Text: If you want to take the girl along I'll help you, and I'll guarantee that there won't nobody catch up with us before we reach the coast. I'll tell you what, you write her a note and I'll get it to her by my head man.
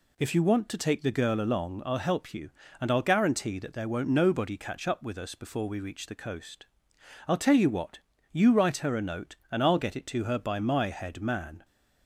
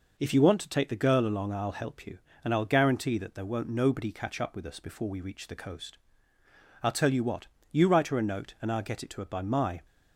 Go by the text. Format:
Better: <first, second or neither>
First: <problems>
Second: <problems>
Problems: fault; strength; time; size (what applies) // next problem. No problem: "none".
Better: first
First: none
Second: stops before "head man"; at 9.8 s